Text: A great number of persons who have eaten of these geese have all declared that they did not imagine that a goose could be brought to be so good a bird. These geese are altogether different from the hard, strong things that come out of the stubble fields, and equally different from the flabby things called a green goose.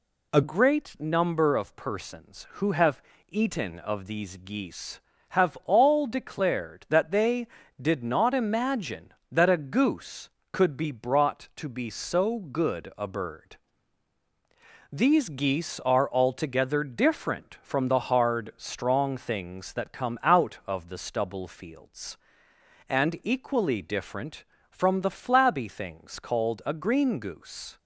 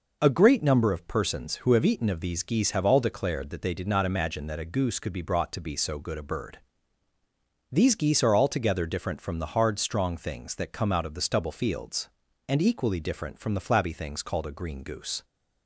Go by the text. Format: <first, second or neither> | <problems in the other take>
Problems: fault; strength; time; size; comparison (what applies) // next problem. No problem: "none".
second | changes voice at "great"; from 0.4 s on; 27.3 s long // pauses between "have" and "eaten"; slight; at 3.0 s; 0.28 s long